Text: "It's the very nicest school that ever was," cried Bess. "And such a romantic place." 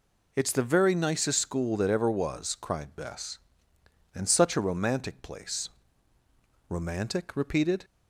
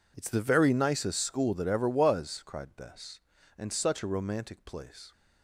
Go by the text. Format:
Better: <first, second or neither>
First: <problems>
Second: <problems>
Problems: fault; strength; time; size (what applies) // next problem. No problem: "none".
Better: second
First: goes on to say "Romantic repeated"; noticeable; from 6.7 s on; 1.1 s long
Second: none